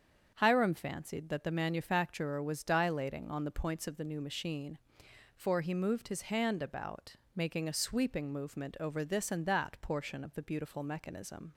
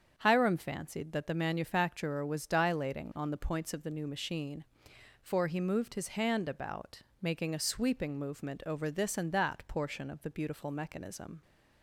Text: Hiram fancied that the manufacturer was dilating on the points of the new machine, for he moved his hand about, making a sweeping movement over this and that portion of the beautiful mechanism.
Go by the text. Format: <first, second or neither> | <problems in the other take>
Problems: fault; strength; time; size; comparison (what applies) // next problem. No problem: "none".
neither | starts louder than the rest; strong; the same in both